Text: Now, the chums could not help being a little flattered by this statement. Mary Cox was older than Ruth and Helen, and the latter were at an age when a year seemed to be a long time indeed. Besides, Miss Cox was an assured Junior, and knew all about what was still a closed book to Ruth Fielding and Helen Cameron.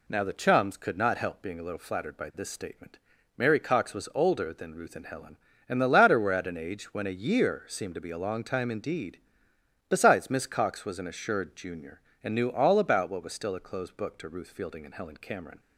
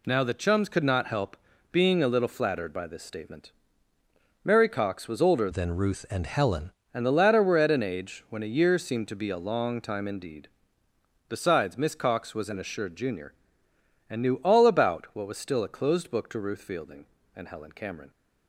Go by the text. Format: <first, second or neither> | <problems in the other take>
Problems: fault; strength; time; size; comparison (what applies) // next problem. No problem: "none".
first | pauses between "help" and "being"; slight; at 1.3 s; 0.36 s long // changes voice from "than" to "Helen"; from 5.5 to 6.7 s; 1.2 s long